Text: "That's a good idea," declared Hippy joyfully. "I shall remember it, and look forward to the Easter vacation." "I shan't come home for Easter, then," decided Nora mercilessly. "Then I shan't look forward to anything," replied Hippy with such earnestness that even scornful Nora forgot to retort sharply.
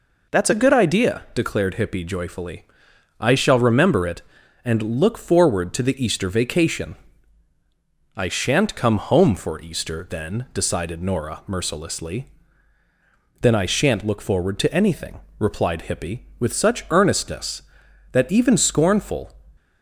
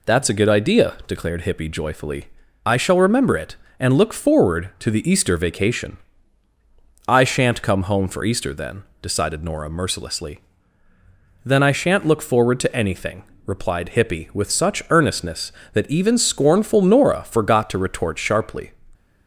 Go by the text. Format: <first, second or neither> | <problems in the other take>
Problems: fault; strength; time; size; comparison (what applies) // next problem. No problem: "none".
second | stops before "Nora forgot to retort sharply"; at 19.5 s